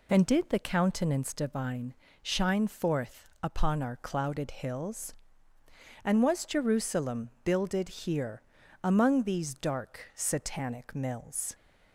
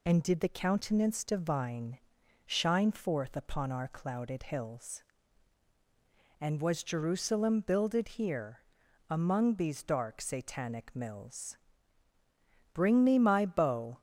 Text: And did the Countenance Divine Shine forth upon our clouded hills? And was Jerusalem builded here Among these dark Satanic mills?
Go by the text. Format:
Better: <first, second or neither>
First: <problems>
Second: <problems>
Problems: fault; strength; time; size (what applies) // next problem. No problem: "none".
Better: first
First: pauses between "Divine" and "Shine"; slight; at 1.9 s; 0.26 s long // pauses between "here" and "Among"; at 8.4 s; 0.40 s long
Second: pauses between "Divine" and "Shine"; noticeable; at 1.9 s; 0.48 s long // pauses between "here" and "Among"; noticeable; at 8.6 s; 0.48 s long // goes on to say "Bring me my bow"; noticeable; from 12.7 s on; 1.2 s long